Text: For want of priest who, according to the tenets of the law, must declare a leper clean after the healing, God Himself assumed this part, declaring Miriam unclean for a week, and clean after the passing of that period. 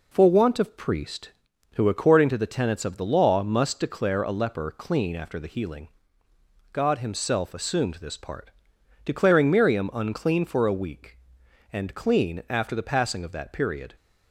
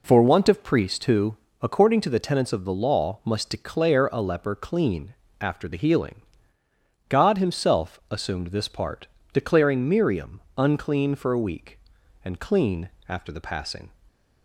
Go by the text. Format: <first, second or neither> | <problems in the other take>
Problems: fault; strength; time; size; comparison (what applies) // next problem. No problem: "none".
first | pauses between "clean" and "after"; slight; at 5.1 s; 0.26 s long // pauses between "Miriam" and "unclean"; slight; at 10.4 s; 0.18 s long // pauses between "clean" and "after"; slight; at 12.8 s; 0.20 s long // stops before "of that period"; at 14.0 s